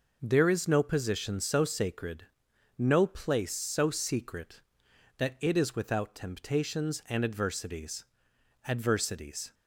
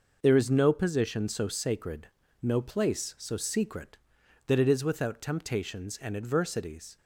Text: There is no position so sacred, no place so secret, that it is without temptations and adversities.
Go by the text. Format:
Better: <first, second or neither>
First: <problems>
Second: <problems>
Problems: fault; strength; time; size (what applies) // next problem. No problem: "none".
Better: second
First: says "adversities" twice; at 8.6 s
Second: none